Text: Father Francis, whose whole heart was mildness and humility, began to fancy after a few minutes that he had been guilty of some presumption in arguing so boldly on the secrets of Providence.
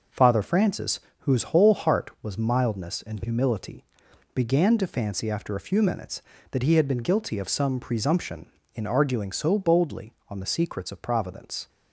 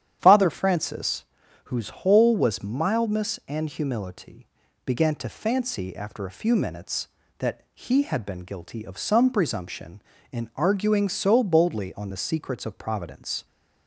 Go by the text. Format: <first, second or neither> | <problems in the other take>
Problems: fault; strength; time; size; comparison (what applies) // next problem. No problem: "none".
first | starts louder than the rest; strong; until 1.2 s; 10 dB // skips "heart"; at 2.3 s